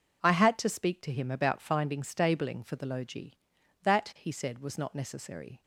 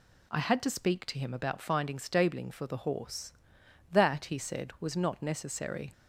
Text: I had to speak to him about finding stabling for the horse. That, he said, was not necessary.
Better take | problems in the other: second | says "logi" for "horse"; at 2.8 s

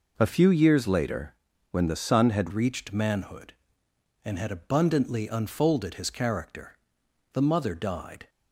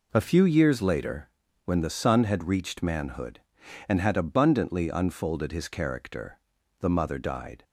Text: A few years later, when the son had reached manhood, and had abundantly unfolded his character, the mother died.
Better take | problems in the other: second | changes voice at "reached"; from 2.5 s on; 5.7 s long

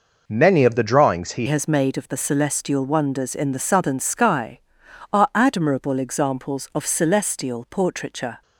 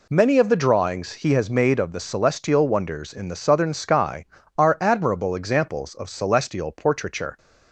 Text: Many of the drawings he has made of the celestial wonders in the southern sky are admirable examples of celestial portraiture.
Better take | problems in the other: second | changes voice at "has"; from 1.4 s on; 7.0 s long

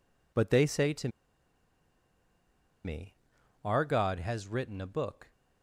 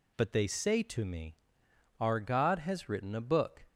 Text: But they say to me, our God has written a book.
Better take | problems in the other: second | pauses between "to" and "me"; strong; at 1.0 s; 1.7 s long

